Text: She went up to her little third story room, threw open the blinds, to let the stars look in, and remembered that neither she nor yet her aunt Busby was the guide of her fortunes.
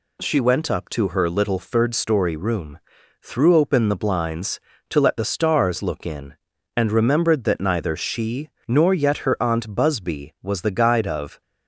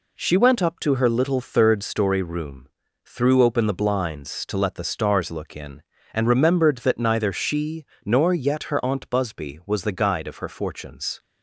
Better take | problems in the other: second | pauses between "she" and "nor"; slight; at 8.5 s; 0.18 s long; slight in the second // stops before "her fortunes"; at 11.4 s

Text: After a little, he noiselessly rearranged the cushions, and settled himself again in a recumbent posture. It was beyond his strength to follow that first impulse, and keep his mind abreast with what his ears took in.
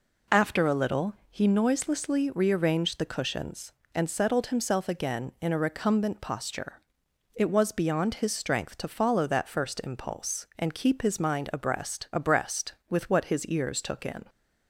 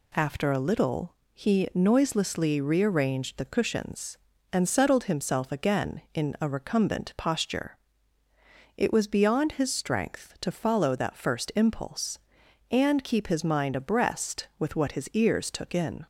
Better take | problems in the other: second | says "abreast" twice; at 12.1 s

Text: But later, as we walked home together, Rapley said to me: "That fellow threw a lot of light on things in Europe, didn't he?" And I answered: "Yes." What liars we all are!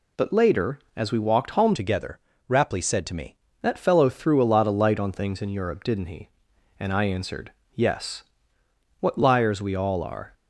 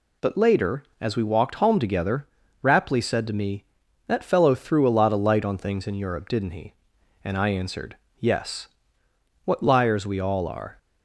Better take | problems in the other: second | changes voice from "together" to "me"; from 1.7 to 3.3 s; 1.6 s long

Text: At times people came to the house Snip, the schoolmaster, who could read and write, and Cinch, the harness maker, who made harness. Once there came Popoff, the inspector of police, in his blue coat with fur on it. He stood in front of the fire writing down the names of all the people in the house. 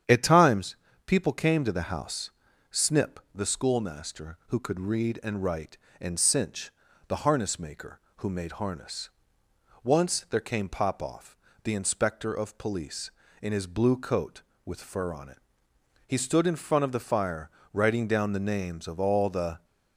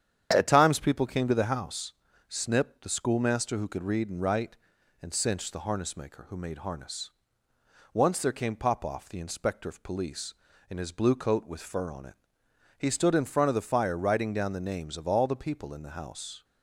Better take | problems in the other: second | starts louder than the rest; strong; until 1.3 s; 9 dB; strong in the second // pauses between "times" and "people"; slight; at 0.7 s; 0.30 s long // pauses between "house" and "Snip"; at 2.3 s; 0.40 s long; also in the second // pauses between "fire" and "writing"; slight; at 17.4 s; 0.24 s long // stops before "people in the house"; at 19.6 s

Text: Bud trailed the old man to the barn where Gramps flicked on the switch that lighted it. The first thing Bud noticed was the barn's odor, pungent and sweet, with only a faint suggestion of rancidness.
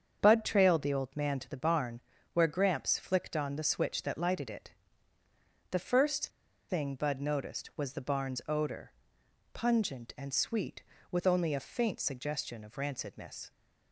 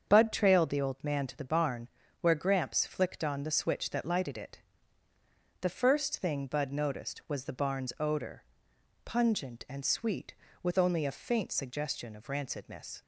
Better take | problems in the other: second | starts louder than the rest; strong; until 1.2 s; 7 dB; strong in the second // pauses between "barn" and "where"; slight; at 2.0 s; 0.32 s long; slight in the second // pauses between "first" and "thing"; at 6.2 s; 0.41 s long

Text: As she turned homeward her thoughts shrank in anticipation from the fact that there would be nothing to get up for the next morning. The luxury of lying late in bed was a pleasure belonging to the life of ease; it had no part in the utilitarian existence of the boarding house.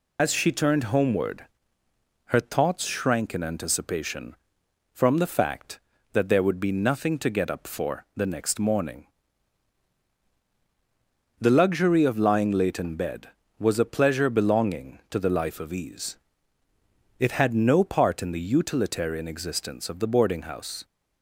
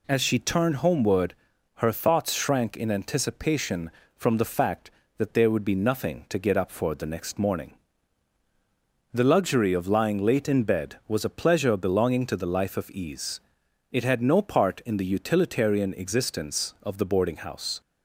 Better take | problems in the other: second | loses the start of "As"; at 0.1 s; 70 ms // pauses between "homeward" and "her"; noticeable; at 1.4 s; 0.82 s long; also in the second

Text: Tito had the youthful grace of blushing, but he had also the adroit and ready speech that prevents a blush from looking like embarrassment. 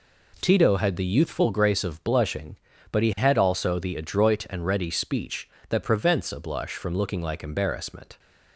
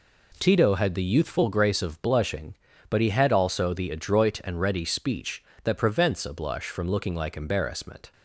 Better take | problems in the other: neither | none

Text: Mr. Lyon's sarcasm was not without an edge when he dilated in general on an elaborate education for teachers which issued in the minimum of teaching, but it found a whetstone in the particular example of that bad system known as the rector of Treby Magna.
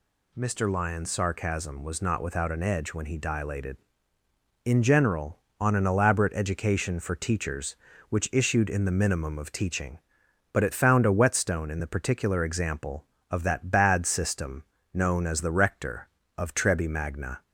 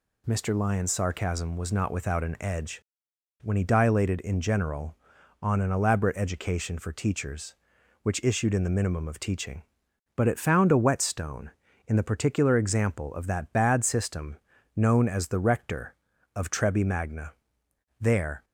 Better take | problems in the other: first | pauses between "edge" and "when"; noticeable; at 2.8 s; 0.60 s long // pauses between "system" and "known"; at 14.3 s; 0.40 s long; slight in the first // goes on to say "There"; slight; from 18.0 s on; 0.44 s long

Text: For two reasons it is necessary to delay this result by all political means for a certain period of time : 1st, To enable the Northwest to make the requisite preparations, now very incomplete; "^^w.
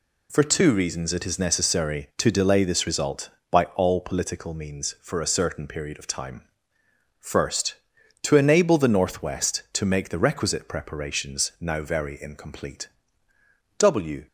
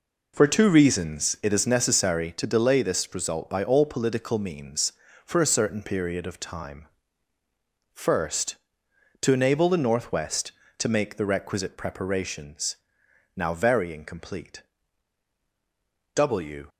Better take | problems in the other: first | starts louder than the rest; noticeable; until 1.5 s; 4.5 dB

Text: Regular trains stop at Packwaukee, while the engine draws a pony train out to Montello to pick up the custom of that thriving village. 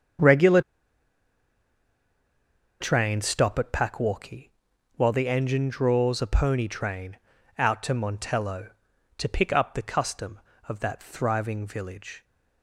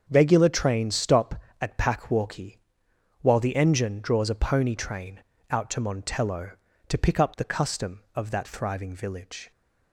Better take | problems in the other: second | starts louder than the rest; strong; until 3.4 s; 7 dB; also in the second // pauses between "Regular" and "trains"; strong; at 0.5 s; 2.2 s long // pauses between "train" and "out"; at 7.1 s; 0.40 s long; slight in the second

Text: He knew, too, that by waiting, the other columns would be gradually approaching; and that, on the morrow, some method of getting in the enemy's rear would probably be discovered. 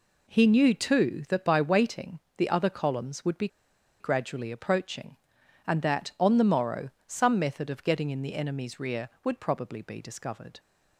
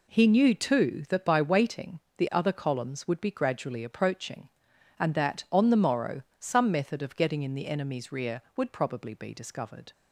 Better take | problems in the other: second | pauses between "be" and "gradually"; noticeable; at 3.4 s; 0.53 s long

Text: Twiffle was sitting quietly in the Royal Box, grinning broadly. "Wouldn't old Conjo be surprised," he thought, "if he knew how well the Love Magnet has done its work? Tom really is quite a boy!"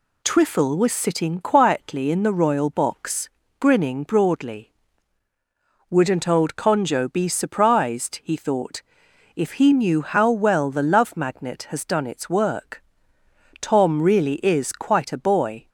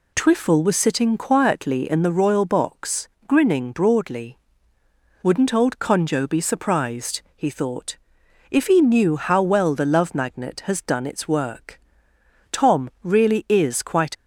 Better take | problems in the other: first | stops before "a boy"; at 14.1 s

